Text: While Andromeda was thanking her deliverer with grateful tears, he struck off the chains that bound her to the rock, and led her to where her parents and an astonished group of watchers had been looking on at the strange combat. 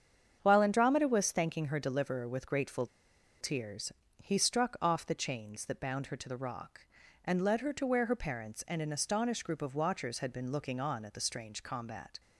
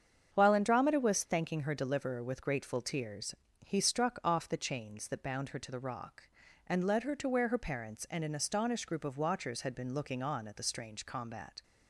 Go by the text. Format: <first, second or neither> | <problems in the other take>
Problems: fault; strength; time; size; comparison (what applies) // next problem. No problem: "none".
second | starts louder than the rest; strong; until 1.4 s; 8 dB; strong in the second // pauses between "grateful" and "tears"; noticeable; at 2.8 s; 0.55 s long